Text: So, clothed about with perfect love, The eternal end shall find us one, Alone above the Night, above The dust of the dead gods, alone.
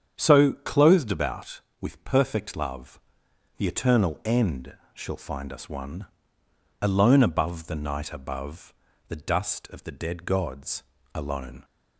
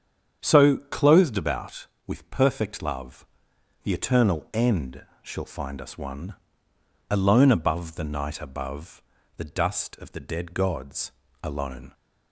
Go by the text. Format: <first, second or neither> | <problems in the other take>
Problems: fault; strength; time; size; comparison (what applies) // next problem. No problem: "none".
neither | starts louder than the rest; strong; the same in both // pauses between "end" and "shall"; slight; the same in both // pauses between "above" and "The"; slight; the same in both